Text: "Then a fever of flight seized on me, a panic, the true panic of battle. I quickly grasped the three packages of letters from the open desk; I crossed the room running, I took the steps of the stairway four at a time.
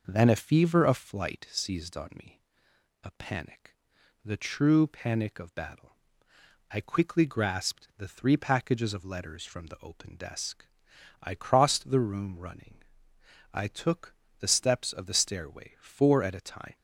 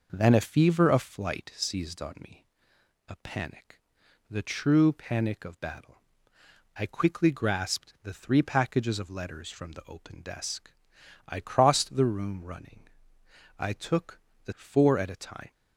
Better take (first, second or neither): first